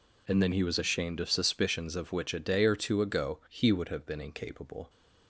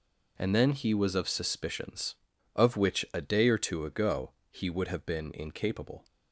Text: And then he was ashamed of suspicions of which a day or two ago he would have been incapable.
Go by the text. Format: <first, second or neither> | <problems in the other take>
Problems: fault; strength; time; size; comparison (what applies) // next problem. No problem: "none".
first | skips "ashamed"; at 1.1 s // pauses between "ago" and "he"; slight; at 4.3 s; 0.18 s long